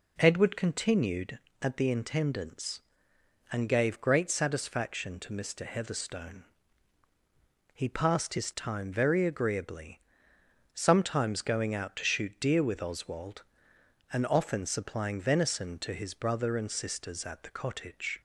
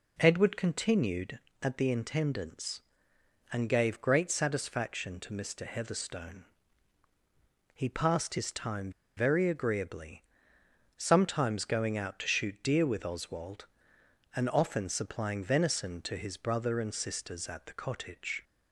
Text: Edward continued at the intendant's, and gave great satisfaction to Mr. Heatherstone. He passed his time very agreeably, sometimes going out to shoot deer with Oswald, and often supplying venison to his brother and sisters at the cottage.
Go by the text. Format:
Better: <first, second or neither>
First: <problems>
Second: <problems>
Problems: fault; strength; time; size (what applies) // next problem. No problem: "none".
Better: first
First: none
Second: pauses between "time" and "very"; slight; at 8.9 s; 0.25 s long